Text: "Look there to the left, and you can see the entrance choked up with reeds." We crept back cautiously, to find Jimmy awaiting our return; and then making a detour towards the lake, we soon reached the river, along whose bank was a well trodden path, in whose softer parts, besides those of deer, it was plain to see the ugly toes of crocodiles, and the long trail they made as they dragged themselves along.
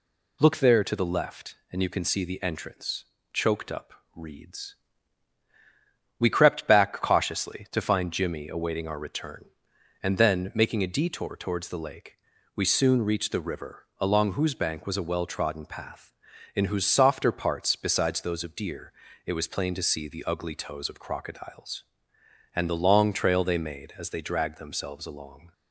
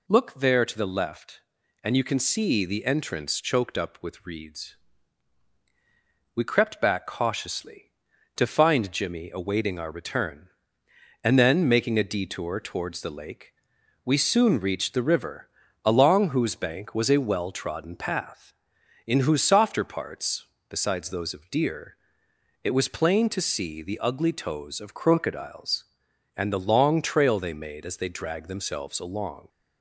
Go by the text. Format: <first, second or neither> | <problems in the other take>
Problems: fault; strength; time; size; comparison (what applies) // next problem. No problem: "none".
second | pauses between "entrance" and "choked"; slight; at 3.0 s; 0.28 s long // skips "with"; at 4.0 s